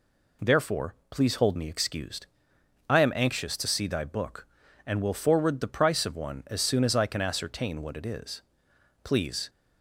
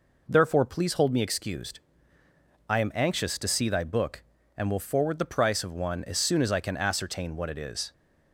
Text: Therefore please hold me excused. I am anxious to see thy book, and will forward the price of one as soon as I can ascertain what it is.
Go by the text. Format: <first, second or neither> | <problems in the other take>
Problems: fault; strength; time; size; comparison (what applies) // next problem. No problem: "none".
second | pauses between "Therefore" and "please"; slight; at 0.9 s; 0.16 s long // goes on to say "Please"; slight; from 9.0 s on; 0.46 s long